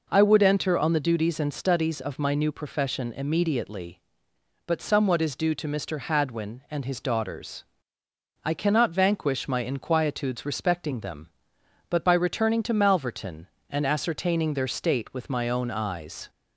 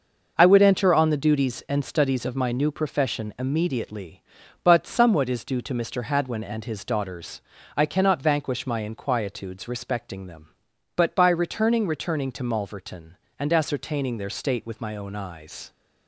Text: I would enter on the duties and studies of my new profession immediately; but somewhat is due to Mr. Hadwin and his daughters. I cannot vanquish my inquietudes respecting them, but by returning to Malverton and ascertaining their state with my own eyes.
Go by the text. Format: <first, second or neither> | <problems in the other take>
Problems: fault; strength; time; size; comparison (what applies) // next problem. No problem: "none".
first | starts louder than the rest; noticeable; until 1.3 s; 6 dB // says "returning" twice; at 11.8 s